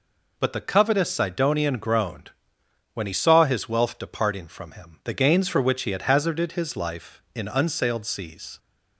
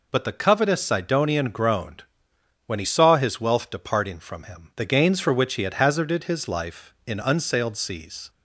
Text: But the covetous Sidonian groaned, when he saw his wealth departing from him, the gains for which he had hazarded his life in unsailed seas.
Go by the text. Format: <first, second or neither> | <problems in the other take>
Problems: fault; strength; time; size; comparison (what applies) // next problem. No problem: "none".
neither | none